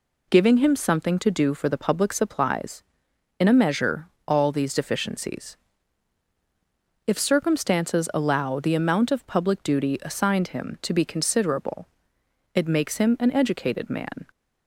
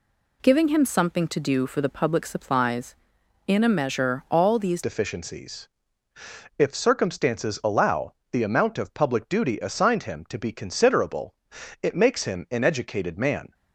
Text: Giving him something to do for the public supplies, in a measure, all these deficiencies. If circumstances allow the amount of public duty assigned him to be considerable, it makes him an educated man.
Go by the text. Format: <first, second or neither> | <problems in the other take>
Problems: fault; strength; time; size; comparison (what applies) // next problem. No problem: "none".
first | changes voice at "deficiencies"; from 4.8 s on; 8.7 s long // pauses between "allow" and "the"; slight; at 8.1 s; 0.16 s long